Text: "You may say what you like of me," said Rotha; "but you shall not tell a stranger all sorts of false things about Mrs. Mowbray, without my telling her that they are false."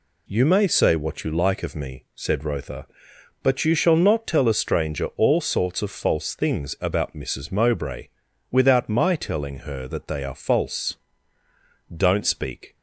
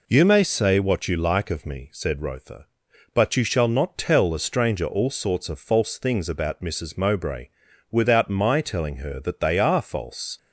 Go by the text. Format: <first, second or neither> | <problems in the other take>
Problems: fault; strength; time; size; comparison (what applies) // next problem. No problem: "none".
second | goes on to say "Don't speak"; noticeable; from 11.9 s on; 0.80 s long